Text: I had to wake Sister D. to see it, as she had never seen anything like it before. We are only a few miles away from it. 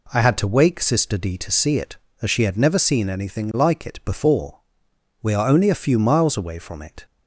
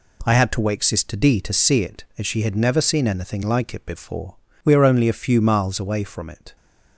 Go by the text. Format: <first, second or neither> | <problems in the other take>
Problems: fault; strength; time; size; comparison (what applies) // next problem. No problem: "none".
neither | none